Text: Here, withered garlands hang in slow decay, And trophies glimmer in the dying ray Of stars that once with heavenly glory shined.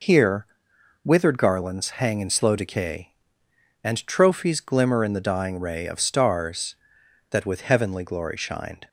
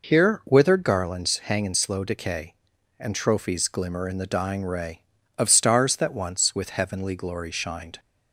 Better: second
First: skips "once"; at 7.4 s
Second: none

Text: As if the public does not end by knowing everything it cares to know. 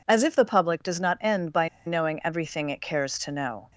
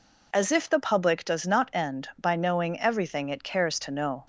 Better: second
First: pauses between "by" and "knowing"; slight; at 1.6 s; 0.18 s long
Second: none

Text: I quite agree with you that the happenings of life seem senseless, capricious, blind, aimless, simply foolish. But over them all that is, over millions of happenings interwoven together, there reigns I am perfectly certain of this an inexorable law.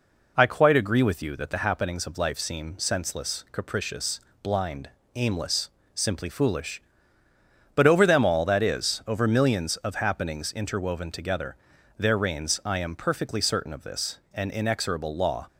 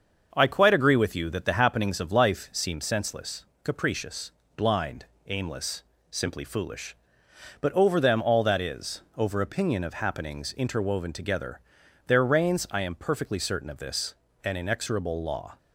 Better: first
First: none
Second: starts louder than the rest; until 1.3 s; 6.5 dB // says "opinion" for "millions"; at 9.3 s // pauses between "this" and "an"; slight; at 14.1 s; 0.28 s long

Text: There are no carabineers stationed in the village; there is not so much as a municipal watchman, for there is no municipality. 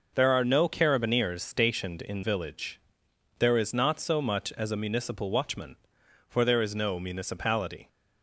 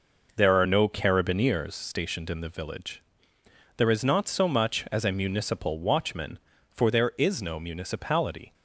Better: second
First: skips "the"; at 2.2 s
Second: none

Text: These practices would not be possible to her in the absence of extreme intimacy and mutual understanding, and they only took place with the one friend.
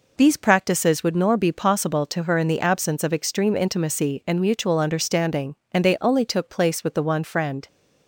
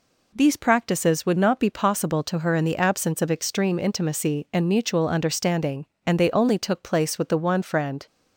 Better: second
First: says "nor" for "not"; at 1.1 s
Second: none

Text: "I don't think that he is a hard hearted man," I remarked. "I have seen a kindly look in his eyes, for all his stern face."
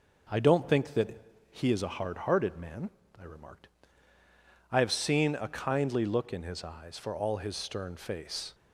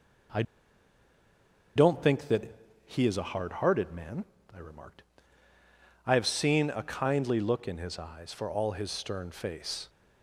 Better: first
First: pauses between "that" and "he"; slight; at 1.2 s; 0.29 s long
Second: pauses between "I" and "don't"; strong; at 0.4 s; 1.3 s long // pauses between "that" and "he"; slight; at 2.5 s; 0.30 s long

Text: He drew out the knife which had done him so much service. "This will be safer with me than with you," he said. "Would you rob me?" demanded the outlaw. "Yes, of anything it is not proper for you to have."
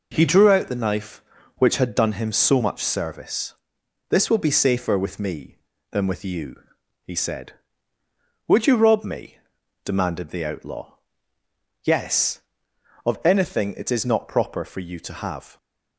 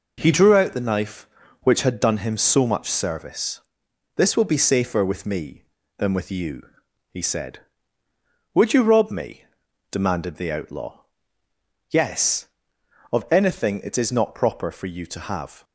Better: neither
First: none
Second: none

